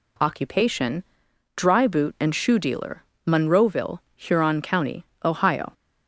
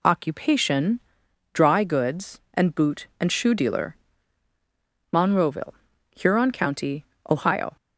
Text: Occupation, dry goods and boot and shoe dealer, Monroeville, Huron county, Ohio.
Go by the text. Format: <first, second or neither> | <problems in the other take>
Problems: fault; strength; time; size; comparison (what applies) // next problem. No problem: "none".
second | skips "goods and"; at 1.8 s